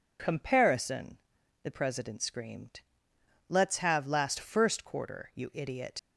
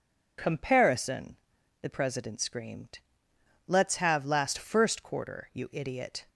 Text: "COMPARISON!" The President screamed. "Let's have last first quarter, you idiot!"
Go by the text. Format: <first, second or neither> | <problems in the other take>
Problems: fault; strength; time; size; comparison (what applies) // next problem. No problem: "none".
second | leaves "idiot" unfinished; at 5.9 s; 105 ms